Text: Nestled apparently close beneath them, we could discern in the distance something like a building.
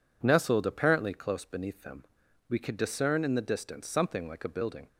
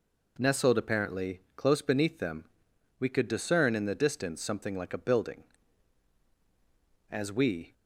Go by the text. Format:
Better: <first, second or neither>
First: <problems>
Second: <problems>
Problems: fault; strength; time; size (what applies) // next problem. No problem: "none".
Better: first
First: none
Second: goes on to say "As we"; noticeable; from 7.1 s on; 0.62 s long